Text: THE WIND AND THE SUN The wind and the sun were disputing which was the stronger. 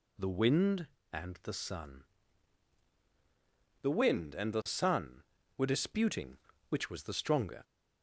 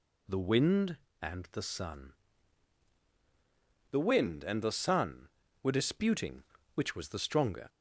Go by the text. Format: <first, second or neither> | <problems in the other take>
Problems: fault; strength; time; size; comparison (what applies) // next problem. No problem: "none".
neither | pauses between "SUN" and "The"; strong; the same in both